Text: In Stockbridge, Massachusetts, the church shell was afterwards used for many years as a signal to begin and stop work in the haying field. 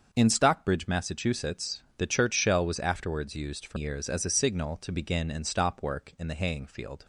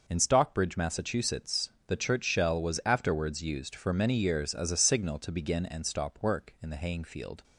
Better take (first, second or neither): second